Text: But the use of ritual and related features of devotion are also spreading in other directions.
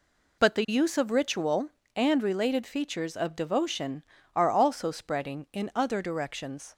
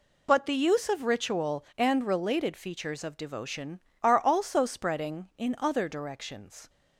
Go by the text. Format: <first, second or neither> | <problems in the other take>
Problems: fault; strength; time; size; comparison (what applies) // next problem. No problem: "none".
neither | none